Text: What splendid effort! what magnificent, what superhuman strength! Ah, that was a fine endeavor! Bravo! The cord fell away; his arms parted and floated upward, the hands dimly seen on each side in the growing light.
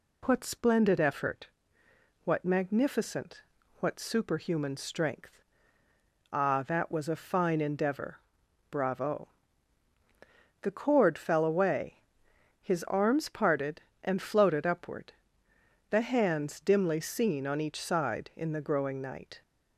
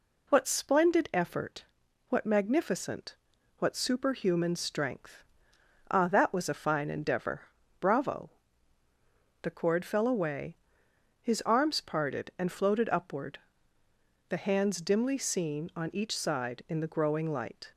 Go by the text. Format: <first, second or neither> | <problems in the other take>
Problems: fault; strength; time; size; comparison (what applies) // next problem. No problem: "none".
second | says "night" for "light"; at 19.0 s